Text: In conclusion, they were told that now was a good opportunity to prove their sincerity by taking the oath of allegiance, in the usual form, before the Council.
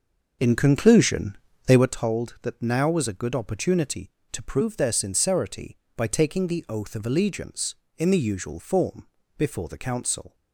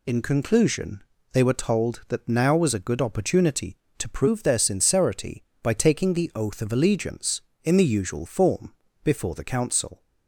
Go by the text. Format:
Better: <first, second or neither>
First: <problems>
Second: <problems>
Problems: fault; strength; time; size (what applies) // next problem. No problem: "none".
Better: second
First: starts louder than the rest; noticeable; until 1.9 s; 6 dB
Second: none